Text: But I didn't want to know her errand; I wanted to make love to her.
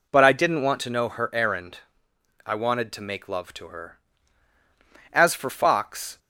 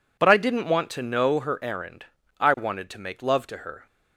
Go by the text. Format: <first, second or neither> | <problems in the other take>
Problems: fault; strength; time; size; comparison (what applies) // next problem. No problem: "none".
second | goes on to say "As for Fox"; noticeable; from 5.1 s on; 1.0 s long